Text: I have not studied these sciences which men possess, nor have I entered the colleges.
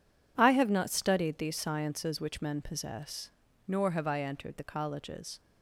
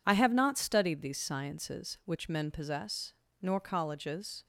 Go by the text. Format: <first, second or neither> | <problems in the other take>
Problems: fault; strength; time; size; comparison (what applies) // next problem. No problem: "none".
first | skips "have I entered the"; at 3.5 s